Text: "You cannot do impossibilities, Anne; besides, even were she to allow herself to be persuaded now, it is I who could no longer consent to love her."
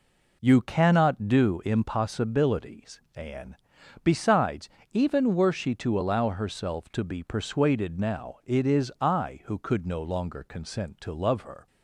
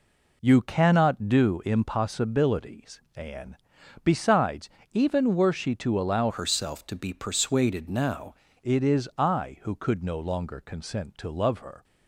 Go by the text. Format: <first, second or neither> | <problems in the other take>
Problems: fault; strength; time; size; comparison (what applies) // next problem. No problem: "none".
first | changes voice from "herself" to "now"; from 6.2 to 8.3 s; 2.1 s long